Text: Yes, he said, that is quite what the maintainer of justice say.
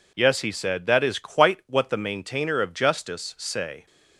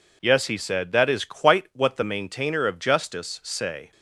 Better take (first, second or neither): neither